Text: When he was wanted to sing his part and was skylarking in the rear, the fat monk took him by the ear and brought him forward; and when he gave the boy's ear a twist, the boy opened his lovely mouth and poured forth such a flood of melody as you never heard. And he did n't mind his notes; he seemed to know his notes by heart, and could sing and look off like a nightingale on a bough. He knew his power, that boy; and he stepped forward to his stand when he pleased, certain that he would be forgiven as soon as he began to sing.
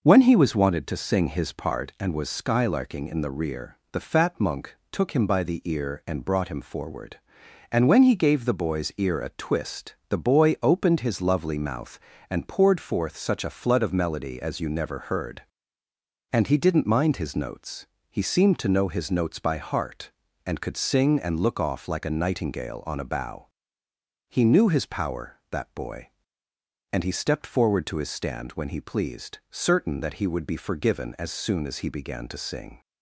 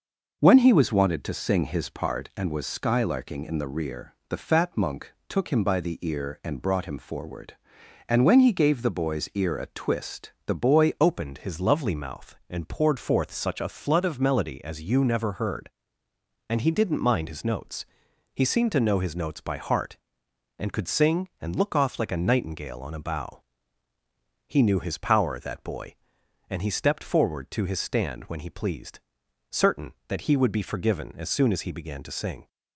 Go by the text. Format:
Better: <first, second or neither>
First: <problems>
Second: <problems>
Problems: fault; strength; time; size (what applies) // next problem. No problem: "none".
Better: first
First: pauses between "monk" and "took"; slight; at 4.7 s; 0.16 s long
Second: pauses between "monk" and "took"; slight; at 5.1 s; 0.16 s long // changes voice at "opened"; from 10.9 s on; 21.5 s long